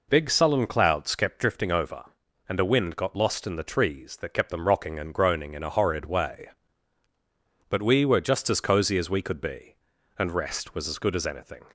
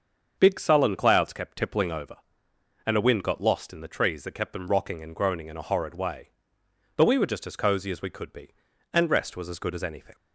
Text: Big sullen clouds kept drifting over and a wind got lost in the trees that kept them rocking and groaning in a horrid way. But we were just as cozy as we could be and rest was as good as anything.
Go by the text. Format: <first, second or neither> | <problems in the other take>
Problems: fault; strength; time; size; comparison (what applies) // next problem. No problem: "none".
first | starts louder than the rest; until 1.3 s; 7 dB // says "tippling" for "drifting"; at 1.5 s